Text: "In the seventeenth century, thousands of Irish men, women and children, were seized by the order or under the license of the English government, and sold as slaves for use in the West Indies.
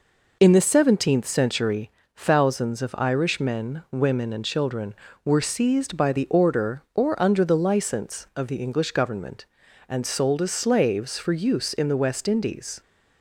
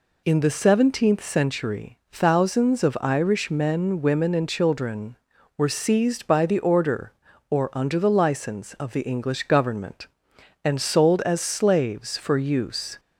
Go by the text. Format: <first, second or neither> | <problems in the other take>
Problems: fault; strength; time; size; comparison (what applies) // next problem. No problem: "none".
first | stops before "in the West Indies"; at 12.9 s